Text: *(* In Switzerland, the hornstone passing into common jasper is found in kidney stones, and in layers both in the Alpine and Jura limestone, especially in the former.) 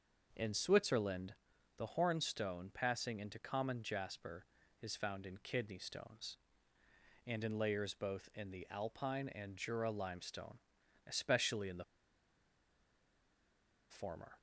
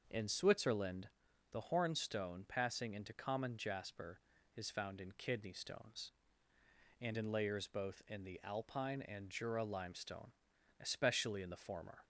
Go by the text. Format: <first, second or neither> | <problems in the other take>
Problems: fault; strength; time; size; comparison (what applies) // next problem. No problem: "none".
second | starts louder than the rest; noticeable; until 1.3 s; 6 dB; noticeable in the second // pauses between "the" and "former"; strong; at 11.8 s; 2.0 s long